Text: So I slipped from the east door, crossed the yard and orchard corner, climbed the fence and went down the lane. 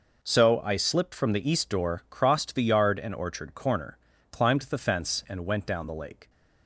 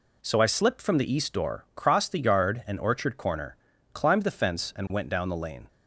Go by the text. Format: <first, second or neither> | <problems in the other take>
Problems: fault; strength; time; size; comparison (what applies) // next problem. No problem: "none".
second | says "lake" for "lane"; at 5.9 s